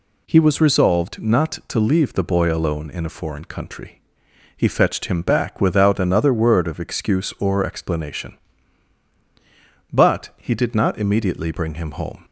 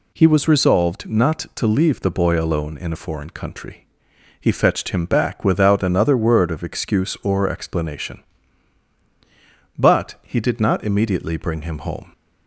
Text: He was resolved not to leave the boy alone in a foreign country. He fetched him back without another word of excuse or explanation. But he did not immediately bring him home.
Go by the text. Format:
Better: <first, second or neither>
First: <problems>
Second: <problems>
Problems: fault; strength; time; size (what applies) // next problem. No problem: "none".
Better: neither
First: none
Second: none